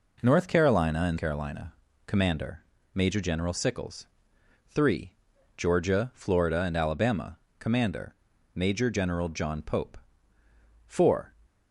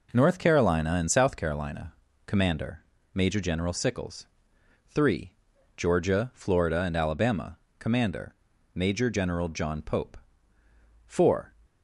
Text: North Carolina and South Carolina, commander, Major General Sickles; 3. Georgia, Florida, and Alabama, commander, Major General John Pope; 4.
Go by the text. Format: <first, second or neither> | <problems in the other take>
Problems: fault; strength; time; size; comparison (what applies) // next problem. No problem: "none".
second | skips "South"; at 1.1 s